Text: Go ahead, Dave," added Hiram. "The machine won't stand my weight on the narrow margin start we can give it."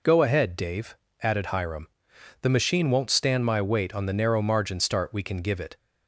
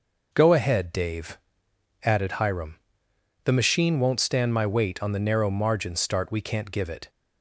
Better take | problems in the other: first | says "can't" for "can"; at 6.3 s

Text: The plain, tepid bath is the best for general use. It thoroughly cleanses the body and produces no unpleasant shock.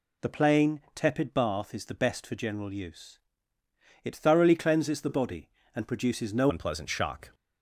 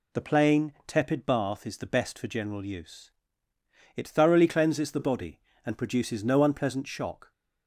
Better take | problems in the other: second | changes voice at "unpleasant"; from 6.4 s on; 0.9 s long

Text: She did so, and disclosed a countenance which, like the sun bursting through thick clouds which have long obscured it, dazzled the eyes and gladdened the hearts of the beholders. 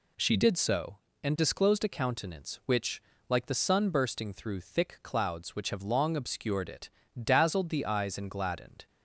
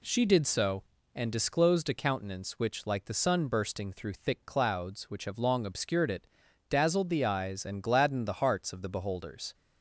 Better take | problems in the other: second | stops before "the hearts of the beholders"; at 8.8 s

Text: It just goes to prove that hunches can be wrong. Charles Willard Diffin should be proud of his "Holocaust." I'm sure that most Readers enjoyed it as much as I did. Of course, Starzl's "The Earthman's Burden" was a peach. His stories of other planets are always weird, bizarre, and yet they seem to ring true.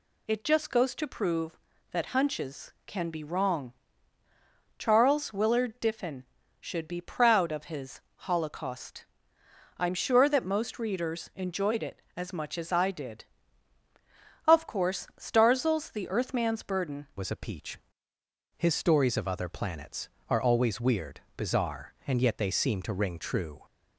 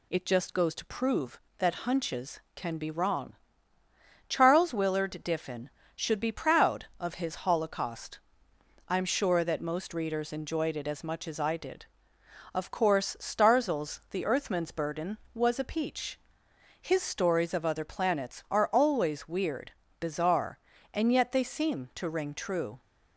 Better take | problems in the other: second | pauses between "his" and "Holocaust"; slight; at 7.9 s; 0.20 s long // changes voice at "was"; from 17.1 s on; 6.5 s long

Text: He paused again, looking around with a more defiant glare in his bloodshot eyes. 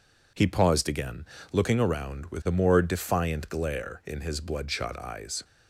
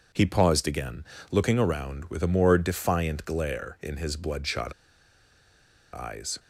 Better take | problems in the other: first | pauses between "bloodshot" and "eyes"; at 4.7 s; 1.2 s long

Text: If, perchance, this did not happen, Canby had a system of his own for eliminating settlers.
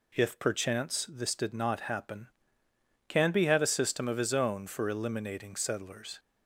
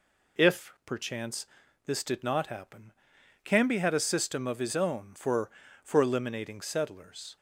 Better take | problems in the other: first | says "for" twice; at 5.8 s

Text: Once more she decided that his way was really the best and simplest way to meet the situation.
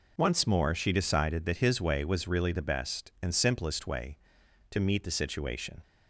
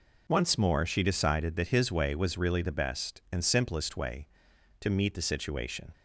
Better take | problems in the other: neither | none

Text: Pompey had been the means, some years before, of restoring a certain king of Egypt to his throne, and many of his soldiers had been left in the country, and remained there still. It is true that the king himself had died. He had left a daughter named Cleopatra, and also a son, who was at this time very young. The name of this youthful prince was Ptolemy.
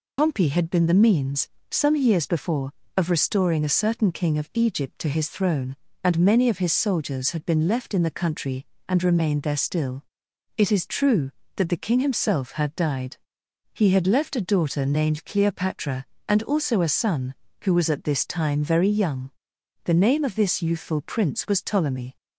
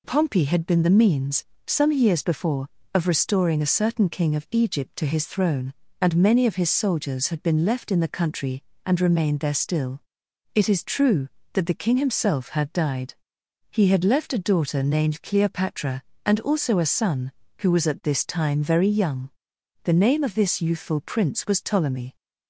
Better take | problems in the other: second | loses the start of "Pompey"; at 0.1 s; 95 ms

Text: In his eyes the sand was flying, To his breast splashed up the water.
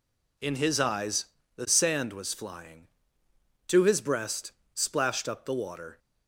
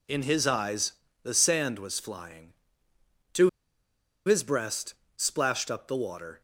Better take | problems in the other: first | pauses between "eyes" and "the"; slight; at 0.9 s; 0.30 s long; slight in the first // pauses between "To" and "his"; noticeable; at 3.4 s; 0.77 s long // pauses between "breast" and "splashed"; slight; at 4.9 s; 0.20 s long; slight in the first

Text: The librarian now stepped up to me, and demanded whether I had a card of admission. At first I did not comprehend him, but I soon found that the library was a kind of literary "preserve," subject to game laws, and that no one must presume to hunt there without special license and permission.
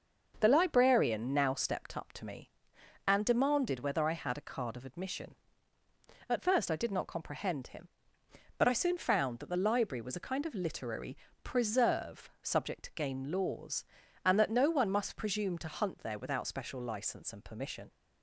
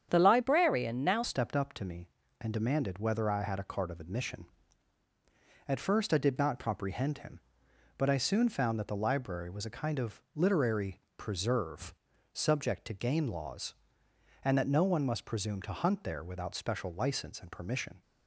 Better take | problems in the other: first | starts louder than the rest; strong; until 1.1 s; 8.5 dB; also in the first // changes voice at "stepped"; from 1.2 s on; 16.8 s long // pauses between "literary" and "preserve"; slight; at 10.9 s; 0.18 s long; slight in the first

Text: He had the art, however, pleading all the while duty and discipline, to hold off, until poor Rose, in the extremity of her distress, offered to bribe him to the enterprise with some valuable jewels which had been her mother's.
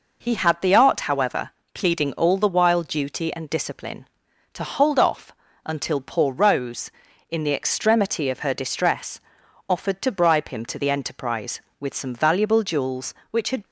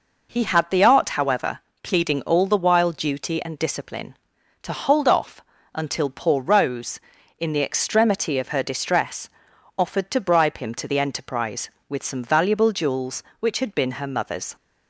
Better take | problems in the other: second | stops before "been her mother's"; at 13.6 s

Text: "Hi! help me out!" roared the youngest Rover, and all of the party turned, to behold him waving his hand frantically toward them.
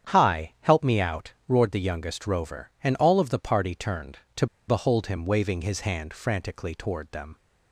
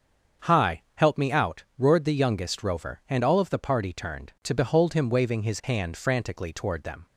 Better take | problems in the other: second | starts louder than the rest; strong; until 1.1 s; 8.5 dB; also in the second // pauses between "to" and "behold"; slight; at 4.4 s; 0.22 s long

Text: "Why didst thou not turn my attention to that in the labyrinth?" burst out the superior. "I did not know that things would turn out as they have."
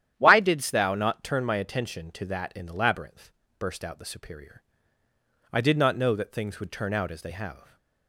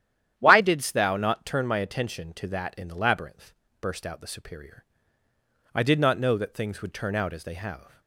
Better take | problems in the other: neither | starts louder than the rest; strong; the same in both

